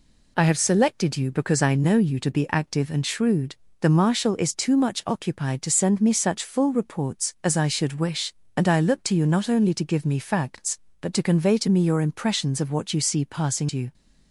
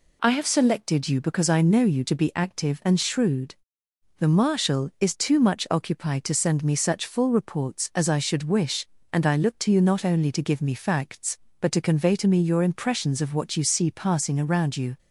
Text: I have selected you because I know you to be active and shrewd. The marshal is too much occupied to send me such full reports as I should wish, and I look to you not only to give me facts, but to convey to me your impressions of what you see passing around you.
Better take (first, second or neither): second